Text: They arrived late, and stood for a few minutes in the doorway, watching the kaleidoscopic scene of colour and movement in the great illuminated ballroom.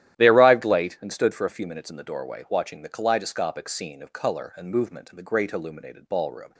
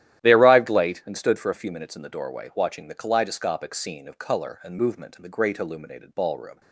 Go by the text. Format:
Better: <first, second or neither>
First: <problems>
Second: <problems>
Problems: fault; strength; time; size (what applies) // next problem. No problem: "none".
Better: neither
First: starts louder than the rest; strong; until 1.2 s; 12.5 dB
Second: starts louder than the rest; strong; until 1.2 s; 12.5 dB